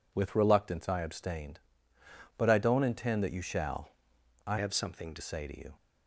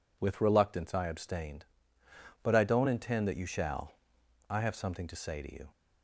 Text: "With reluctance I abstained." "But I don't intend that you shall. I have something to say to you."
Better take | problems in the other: second | changes voice from "have" to "to"; from 4.5 to 5.2 s; 0.7 s long

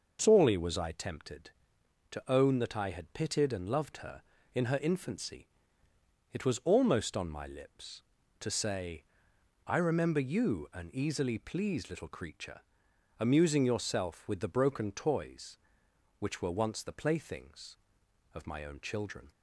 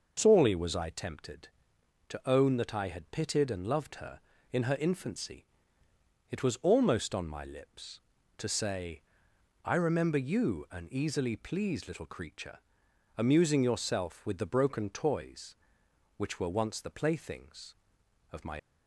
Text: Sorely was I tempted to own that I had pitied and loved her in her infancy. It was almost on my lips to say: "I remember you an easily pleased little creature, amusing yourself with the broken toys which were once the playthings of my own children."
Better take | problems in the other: first | stops before "own children"; at 18.5 s

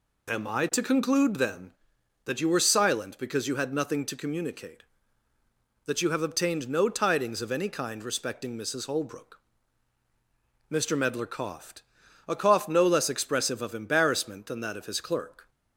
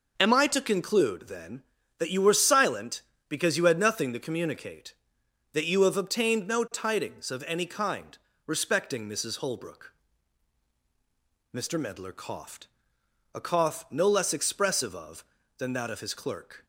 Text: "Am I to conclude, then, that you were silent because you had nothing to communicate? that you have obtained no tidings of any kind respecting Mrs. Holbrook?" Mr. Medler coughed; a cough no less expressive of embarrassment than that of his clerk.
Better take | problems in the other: first | pauses between "kind" and "respecting"; slight; at 8.1 s; 0.30 s long // skips "embarrassment"; at 15.4 s

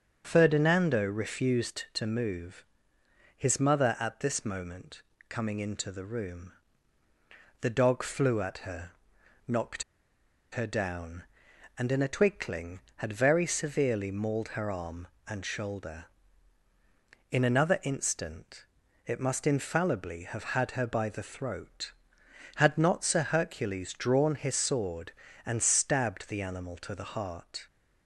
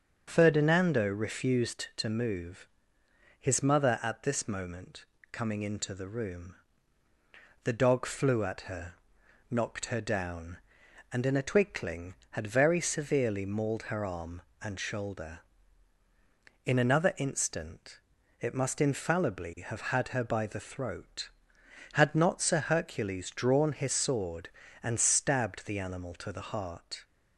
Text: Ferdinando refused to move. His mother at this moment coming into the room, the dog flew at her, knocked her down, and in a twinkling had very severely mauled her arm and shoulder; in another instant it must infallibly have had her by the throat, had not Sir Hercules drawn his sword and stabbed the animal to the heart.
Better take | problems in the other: second | starts louder than the rest; until 1.2 s; 6.5 dB; also in the second // pauses between "moment" and "coming"; slight; at 5.0 s; 0.28 s long; slight in the second // pauses between "knocked" and "her"; noticeable; at 9.8 s; 0.69 s long // pauses between "instant" and "it"; at 18.6 s; 0.40 s long; also in the second

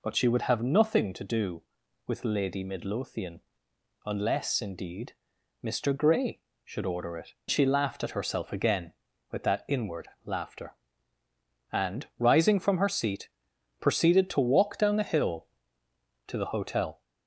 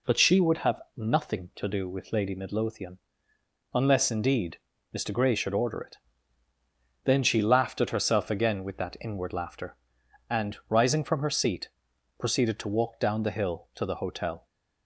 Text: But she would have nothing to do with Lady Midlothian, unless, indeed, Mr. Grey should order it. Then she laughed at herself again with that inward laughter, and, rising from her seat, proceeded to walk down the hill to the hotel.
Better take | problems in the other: second | skips "Then"; at 7.4 s // pauses between "inward" and "laughter"; slight; at 10.0 s; 0.18 s long

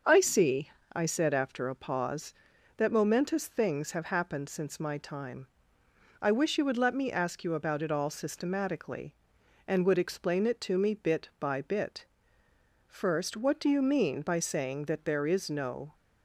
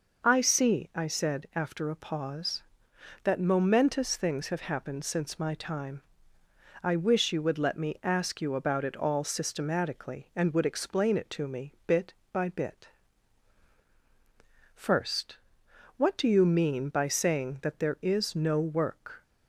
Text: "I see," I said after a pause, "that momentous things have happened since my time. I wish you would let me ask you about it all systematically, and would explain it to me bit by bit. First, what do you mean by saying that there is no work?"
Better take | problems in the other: second | starts louder than the rest; until 1.3 s; 6.5 dB // stops before "work"; at 15.9 s

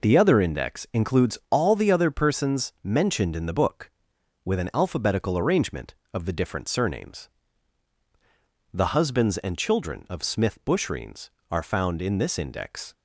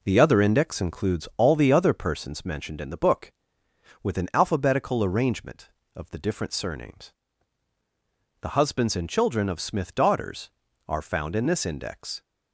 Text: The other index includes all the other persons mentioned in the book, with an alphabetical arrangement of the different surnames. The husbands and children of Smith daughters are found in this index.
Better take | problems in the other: second | says "bushreens" for "daughters"; at 10.6 s

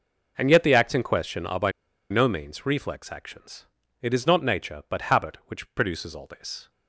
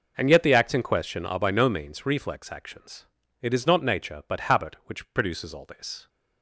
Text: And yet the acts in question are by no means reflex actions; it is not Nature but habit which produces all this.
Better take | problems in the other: second | pauses between "by" and "no"; at 1.7 s; 0.39 s long

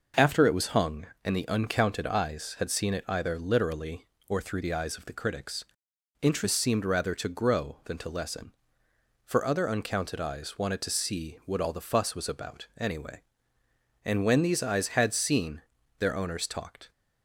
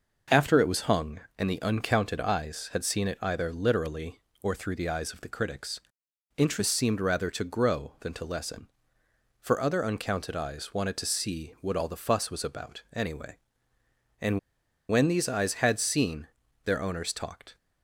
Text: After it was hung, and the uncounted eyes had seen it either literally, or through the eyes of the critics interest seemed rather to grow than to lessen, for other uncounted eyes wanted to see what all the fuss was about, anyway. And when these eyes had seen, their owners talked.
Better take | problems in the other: first | pauses between "critics" and "interest"; noticeable; at 5.8 s; 0.56 s long; noticeable in the first // pauses between "And" and "when"; noticeable; at 14.3 s; 0.50 s long

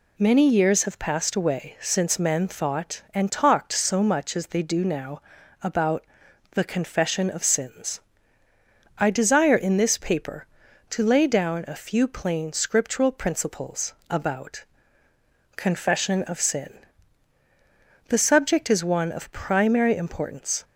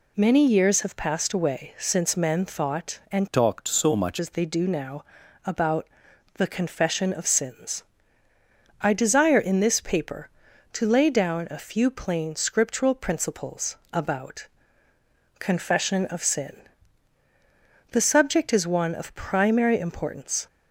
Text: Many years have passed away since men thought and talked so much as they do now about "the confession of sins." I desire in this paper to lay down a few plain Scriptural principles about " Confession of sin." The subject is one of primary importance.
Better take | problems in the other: first | changes voice from "talked" to "much"; from 3.3 to 4.1 s; 0.8 s long // pauses between "now" and "about"; at 5.0 s; 0.40 s long; also in the first // pauses between "about" and "the"; noticeable; at 5.8 s; 0.52 s long; noticeable in the first // pauses between "principles" and "about"; slight; at 13.7 s; 0.16 s long; slight in the first

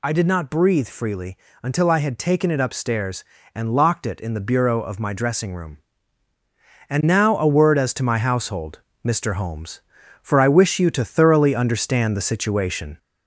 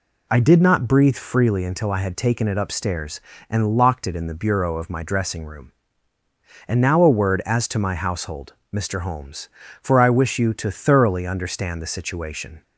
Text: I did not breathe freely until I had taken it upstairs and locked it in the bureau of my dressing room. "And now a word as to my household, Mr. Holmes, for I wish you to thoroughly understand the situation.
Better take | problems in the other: second | gets louder; slight; throughout; 2.5 dB // pauses between "freely" and "until"; slight; at 1.3 s; 0.26 s long

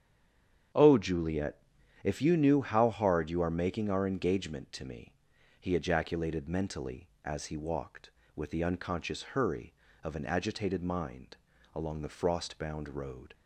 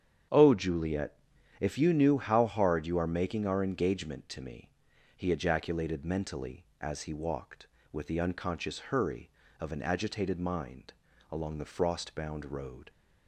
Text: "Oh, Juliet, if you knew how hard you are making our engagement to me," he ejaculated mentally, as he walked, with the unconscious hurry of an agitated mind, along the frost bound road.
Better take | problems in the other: second | stays silent before the first word; slight; until 0.7 s; 0.7 s long // starts louder than the rest; strong; until 2.1 s; 8 dB; strong in the second

